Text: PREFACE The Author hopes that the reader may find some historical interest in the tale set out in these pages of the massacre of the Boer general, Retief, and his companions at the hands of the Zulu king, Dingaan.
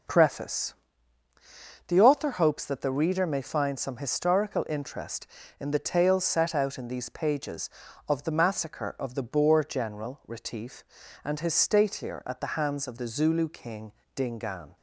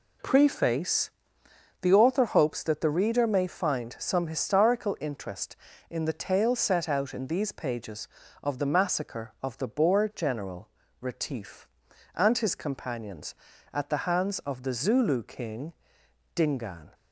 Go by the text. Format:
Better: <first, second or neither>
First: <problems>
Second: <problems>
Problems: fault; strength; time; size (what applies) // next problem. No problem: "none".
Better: second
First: pauses between "PREFACE" and "The"; at 0.7 s; 1.1 s long // says "statelier" for "companions"; at 11.5 s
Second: pauses between "PREFACE" and "The"; noticeable; at 1.1 s; 0.68 s long